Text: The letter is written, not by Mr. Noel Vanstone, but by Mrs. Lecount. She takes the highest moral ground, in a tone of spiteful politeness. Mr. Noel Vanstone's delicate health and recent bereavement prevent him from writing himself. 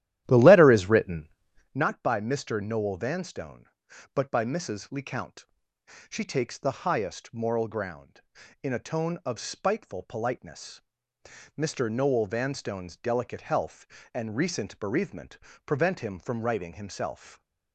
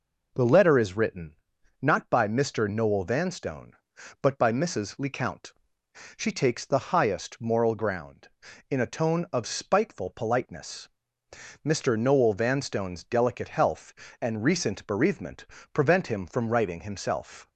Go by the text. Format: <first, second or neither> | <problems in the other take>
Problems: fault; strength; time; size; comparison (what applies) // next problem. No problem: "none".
second | starts louder than the rest; strong; until 1.8 s; 13 dB // pauses between "bereavement" and "prevent"; slight; at 15.3 s; 0.30 s long; slight in the second